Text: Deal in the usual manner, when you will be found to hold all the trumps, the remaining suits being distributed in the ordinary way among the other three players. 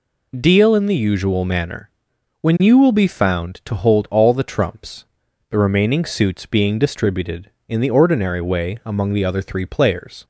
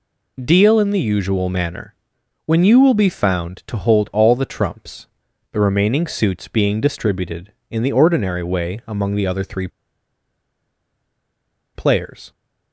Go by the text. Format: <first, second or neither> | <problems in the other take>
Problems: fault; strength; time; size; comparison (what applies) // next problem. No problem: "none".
first | pauses between "three" and "players"; strong; at 9.6 s; 2.0 s long